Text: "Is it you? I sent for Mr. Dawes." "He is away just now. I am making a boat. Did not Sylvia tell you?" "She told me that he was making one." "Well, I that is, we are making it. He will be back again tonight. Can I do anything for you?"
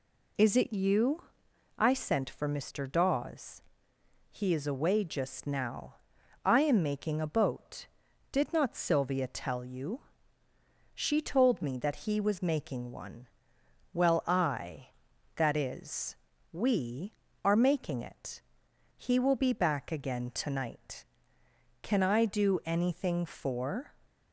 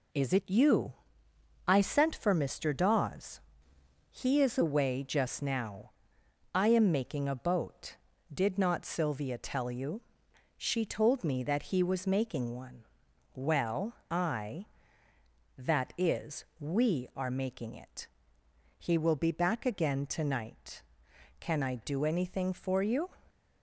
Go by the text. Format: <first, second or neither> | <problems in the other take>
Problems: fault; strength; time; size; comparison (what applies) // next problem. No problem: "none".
second | stops before "you"; at 24.0 s